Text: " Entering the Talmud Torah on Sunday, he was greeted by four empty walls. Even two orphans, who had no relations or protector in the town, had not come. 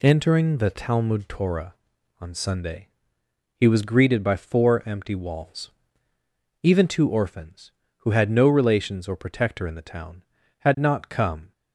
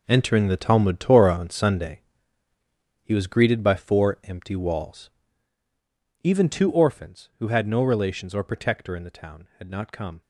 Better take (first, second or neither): first